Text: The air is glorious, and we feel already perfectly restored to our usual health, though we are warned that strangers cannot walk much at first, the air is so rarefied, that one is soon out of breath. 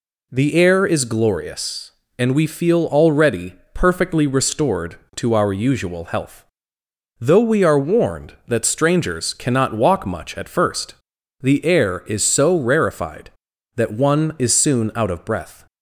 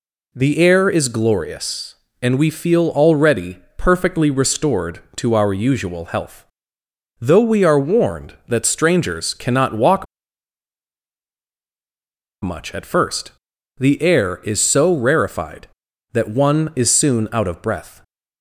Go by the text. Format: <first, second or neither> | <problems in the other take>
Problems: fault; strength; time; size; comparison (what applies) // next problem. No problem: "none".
first | pauses between "already" and "perfectly"; slight; at 3.5 s; 0.18 s long; slight in the first // pauses between "walk" and "much"; strong; at 10.0 s; 2.3 s long